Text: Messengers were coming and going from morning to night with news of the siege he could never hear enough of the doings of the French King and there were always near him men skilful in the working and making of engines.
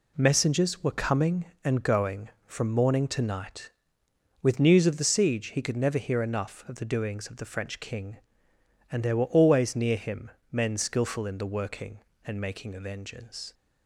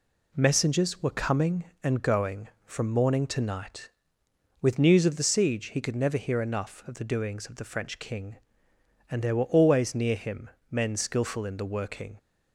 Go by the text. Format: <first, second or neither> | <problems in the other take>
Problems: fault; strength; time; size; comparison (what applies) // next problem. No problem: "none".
first | pauses between "him" and "men"; slight; at 10.4 s; 0.22 s long; slight in the first // stops before "and making of engines"; at 12.1 s